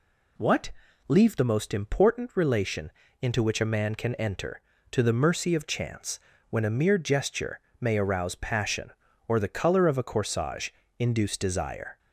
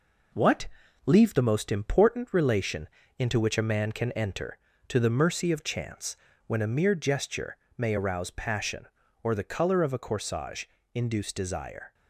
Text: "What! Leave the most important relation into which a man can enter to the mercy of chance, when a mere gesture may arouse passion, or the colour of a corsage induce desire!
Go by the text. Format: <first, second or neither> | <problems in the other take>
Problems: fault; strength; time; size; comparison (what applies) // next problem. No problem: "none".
first | gets quieter; slight; throughout; 3 dB // pauses between "relation" and "into"; slight; at 2.8 s; 0.32 s long; slight in the first // pauses between "gesture" and "may"; slight; at 7.5 s; 0.20 s long; slight in the first // pauses between "corsage" and "induce"; slight; at 10.6 s; 0.28 s long; slight in the first